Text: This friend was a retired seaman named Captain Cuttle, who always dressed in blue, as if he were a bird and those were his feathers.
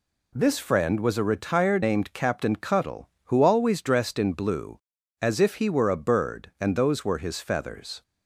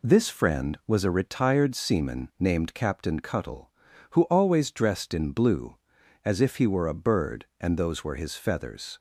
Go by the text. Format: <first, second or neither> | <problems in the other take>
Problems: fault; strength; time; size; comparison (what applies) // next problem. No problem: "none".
second | skips "seaman"; at 1.8 s